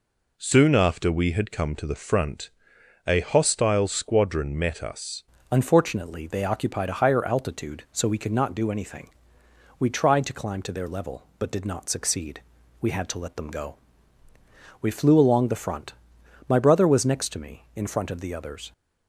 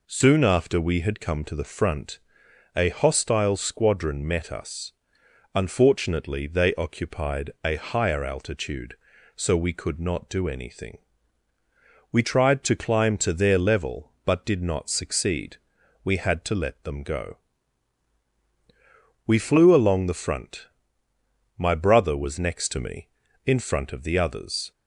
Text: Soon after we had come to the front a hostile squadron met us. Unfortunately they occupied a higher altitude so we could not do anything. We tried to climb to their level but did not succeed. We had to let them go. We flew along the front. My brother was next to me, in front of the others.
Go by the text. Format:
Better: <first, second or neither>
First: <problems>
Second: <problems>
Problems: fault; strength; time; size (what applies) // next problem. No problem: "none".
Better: second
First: pauses between "front" and "a"; noticeable; at 2.5 s; 0.56 s long // changes voice at "Unfortunately"; from 5.4 s on; 13.3 s long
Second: pauses between "front" and "a"; noticeable; at 2.1 s; 0.56 s long